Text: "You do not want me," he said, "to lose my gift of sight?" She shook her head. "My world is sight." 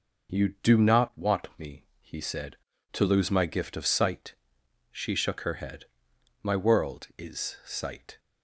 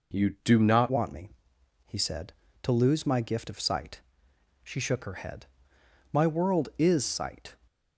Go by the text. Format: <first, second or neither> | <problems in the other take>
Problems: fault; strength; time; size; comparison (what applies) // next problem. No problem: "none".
first | changes voice at "want"; from 0.8 s on; 6.7 s long